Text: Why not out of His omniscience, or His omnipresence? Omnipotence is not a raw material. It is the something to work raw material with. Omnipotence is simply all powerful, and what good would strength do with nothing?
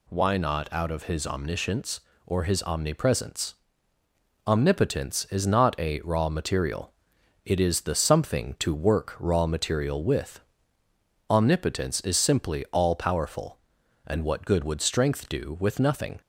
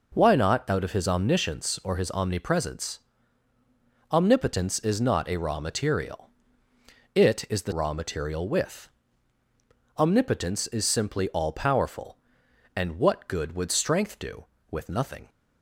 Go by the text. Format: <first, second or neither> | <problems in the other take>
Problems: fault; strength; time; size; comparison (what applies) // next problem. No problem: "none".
first | skips "something to work"; at 7.7 s